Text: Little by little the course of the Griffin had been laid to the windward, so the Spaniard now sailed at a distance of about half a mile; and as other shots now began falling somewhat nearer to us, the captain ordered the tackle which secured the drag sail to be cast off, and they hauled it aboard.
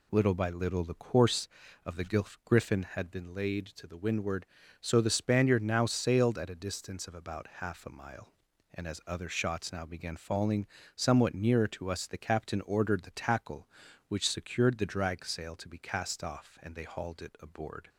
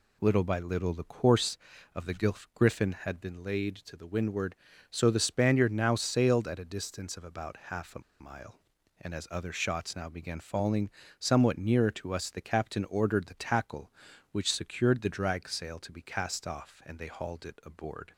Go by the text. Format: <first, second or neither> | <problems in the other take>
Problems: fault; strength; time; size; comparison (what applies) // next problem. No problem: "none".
first | pauses between "the" and "Griffin"; slight; at 2.3 s; 0.20 s long; slight in the first // pauses between "a" and "mile"; slight; at 8.0 s; 0.19 s long // pauses between "falling" and "somewhat"; slight; at 10.9 s; 0.28 s long; slight in the first